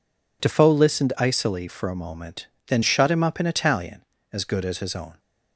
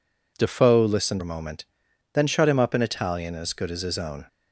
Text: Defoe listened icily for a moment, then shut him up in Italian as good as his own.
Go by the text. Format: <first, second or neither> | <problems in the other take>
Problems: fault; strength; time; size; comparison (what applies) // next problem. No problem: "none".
first | skips "icily for"; at 1.2 s